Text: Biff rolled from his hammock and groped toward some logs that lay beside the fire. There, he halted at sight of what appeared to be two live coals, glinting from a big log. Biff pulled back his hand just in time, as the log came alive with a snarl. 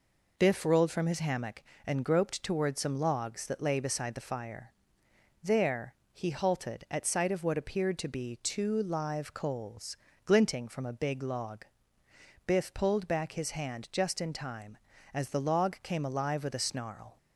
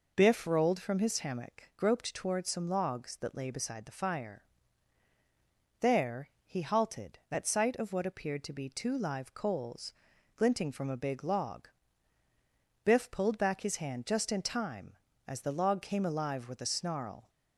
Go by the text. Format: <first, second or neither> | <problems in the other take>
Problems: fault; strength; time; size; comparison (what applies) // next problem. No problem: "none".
first | skips "and"; at 1.7 s